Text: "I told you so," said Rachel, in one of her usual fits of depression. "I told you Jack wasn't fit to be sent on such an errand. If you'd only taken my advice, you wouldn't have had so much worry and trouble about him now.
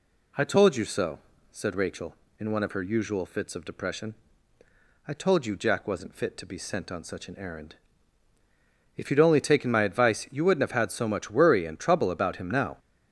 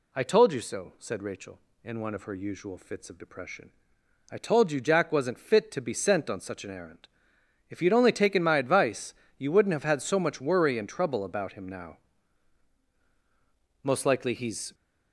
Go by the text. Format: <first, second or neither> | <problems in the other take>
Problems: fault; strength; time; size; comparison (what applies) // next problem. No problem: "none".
first | goes on to say "Most likely he's"; noticeable; from 13.8 s on; 0.90 s long